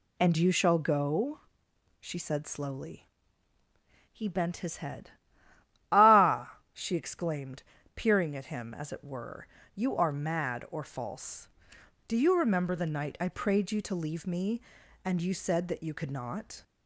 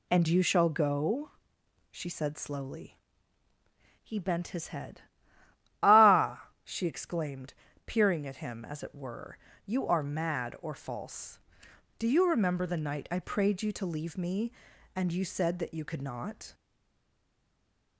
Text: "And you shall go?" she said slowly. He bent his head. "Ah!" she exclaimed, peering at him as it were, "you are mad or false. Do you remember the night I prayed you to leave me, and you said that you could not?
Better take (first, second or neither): first